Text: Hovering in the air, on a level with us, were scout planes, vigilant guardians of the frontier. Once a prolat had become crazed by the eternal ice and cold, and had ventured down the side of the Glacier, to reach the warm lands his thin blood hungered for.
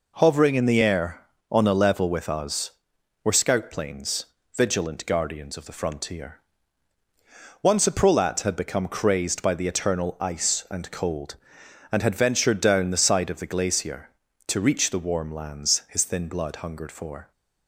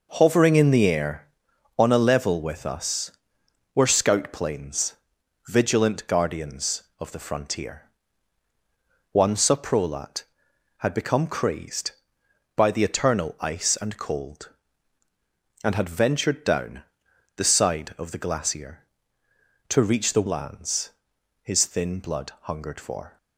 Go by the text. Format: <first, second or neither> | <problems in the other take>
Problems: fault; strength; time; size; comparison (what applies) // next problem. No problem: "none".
first | pauses between "down" and "the"; noticeable; at 16.8 s; 0.54 s long // skips "warm"; at 20.2 s // pauses between "lands" and "his"; noticeable; at 20.8 s; 0.54 s long